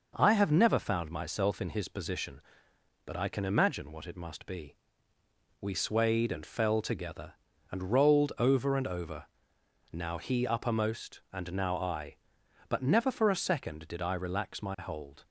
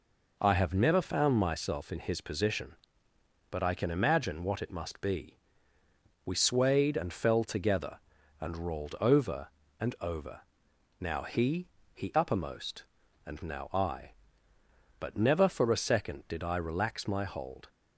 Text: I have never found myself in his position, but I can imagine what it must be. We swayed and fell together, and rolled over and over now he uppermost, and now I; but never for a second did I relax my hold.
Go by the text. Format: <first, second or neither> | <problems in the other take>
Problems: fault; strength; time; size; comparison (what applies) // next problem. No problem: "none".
first | pauses between "over" and "now"; noticeable; at 10.4 s; 0.60 s long; noticeable in the first // says "he" twice; at 11.9 s